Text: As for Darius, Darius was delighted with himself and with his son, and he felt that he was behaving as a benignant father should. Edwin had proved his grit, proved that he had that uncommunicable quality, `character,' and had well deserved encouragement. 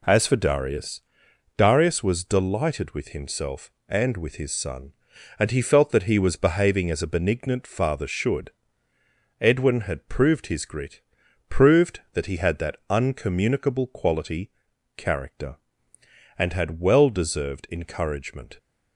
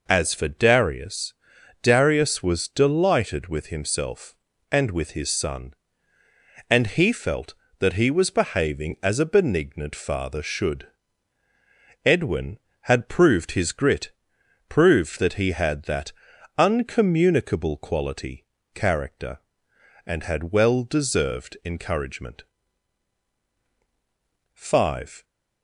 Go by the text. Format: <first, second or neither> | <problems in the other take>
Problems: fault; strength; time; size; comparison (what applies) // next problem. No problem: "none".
first | pauses between "that" and "uncommunicable"; noticeable; at 16.1 s; 0.46 s long // goes on to say "FIVE"; noticeable; from 24.5 s on; 0.70 s long